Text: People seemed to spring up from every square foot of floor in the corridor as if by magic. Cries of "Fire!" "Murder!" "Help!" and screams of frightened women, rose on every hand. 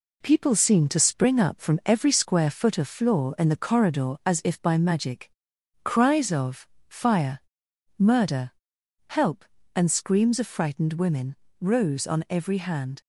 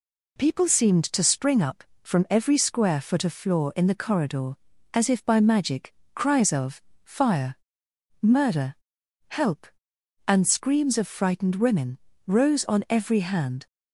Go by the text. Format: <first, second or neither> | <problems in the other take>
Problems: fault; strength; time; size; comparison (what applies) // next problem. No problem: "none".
second | gets quieter; noticeable; throughout; 4 dB // pauses between "of" and "Fire"; slight; at 6.6 s; 0.22 s long; slight in the second